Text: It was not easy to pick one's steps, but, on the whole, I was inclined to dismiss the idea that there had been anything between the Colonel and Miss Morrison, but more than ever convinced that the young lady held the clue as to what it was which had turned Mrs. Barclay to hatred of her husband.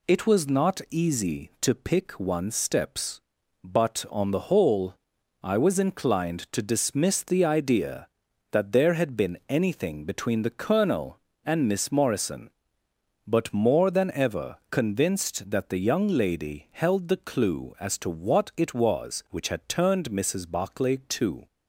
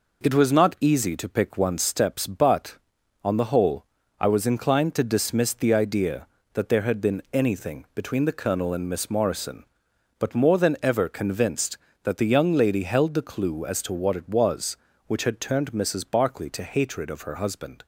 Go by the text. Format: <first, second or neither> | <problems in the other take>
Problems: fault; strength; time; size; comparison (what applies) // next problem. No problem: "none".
second | stops before "hatred of her husband"; at 21.4 s